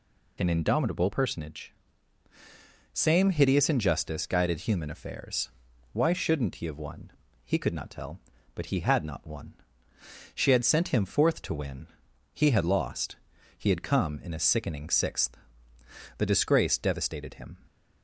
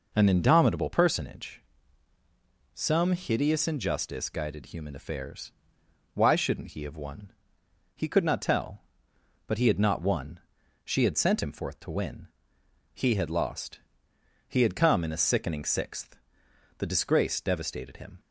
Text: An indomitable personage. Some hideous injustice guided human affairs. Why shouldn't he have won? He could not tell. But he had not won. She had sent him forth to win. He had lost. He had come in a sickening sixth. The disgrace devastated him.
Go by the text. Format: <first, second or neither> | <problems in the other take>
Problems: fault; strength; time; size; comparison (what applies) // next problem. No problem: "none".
second | says "Same" for "Some"; at 2.9 s